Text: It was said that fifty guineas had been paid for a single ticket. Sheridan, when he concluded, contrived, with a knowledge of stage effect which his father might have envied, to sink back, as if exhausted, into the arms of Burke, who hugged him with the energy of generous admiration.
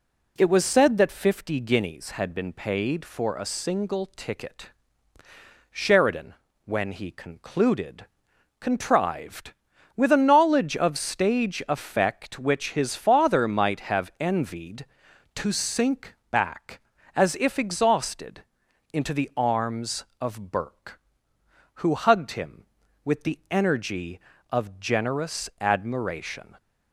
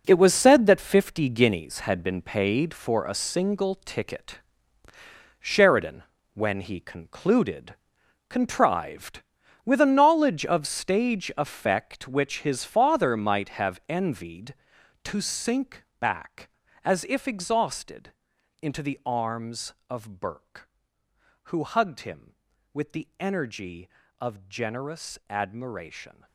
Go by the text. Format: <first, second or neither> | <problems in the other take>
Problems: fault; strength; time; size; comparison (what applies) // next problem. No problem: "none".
first | gets quieter; strong; throughout; 12 dB // pauses between "sink" and "back"; slight; at 15.8 s; 0.16 s long; slight in the first